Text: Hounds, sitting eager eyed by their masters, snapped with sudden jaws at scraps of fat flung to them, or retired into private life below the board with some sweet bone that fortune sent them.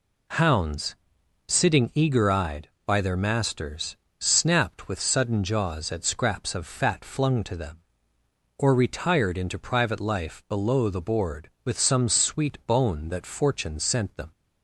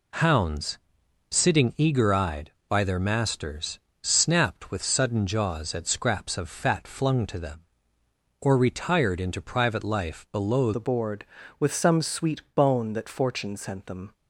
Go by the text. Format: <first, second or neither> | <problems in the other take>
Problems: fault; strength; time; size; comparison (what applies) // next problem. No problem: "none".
first | changes voice at "the"; from 10.7 s on; 3.4 s long